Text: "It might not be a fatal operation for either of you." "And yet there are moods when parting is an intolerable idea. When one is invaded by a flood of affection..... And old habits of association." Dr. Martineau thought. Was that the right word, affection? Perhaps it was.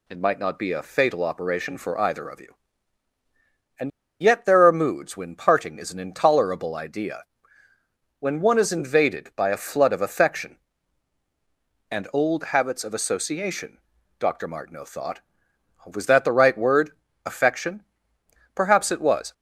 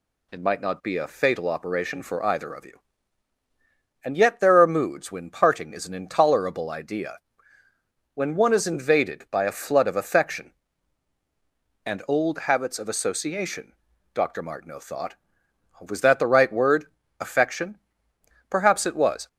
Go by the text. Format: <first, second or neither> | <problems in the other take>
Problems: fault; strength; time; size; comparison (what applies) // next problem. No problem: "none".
second | pauses between "And" and "yet"; slight; at 3.9 s; 0.30 s long